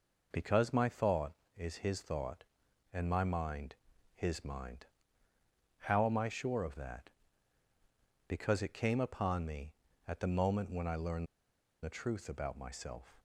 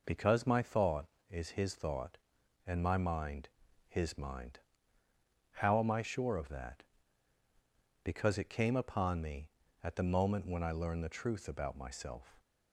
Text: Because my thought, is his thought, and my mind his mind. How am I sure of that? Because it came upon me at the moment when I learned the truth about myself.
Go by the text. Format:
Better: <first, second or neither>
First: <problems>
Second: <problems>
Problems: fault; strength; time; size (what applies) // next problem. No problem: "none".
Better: second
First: pauses between "mind" and "his"; at 3.7 s; 0.40 s long // pauses between "learned" and "the"; noticeable; at 11.2 s; 0.57 s long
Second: pauses between "mind" and "his"; at 3.4 s; 0.40 s long